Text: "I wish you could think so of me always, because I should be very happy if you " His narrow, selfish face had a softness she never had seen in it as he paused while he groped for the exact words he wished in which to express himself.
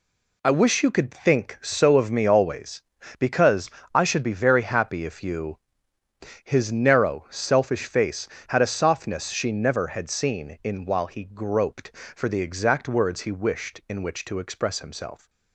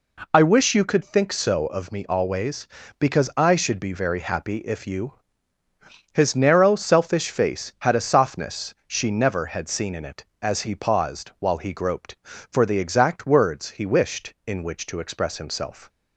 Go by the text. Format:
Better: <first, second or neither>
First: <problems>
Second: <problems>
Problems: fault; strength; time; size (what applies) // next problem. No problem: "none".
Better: second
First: pauses between "because" and "I"; slight; at 3.6 s; 0.24 s long // skips "it as he paused"; at 10.8 s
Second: none